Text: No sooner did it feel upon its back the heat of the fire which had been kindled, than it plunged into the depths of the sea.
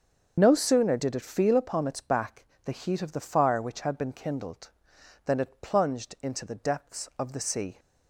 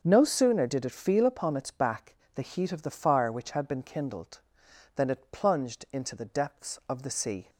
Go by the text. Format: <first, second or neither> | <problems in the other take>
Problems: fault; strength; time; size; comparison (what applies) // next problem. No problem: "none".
second | loses the start of "No"; at 0.3 s; 35 ms // starts louder than the rest; until 1.4 s; 7 dB; also in the second // pauses between "back" and "the"; slight; at 2.4 s; 0.20 s long; slight in the second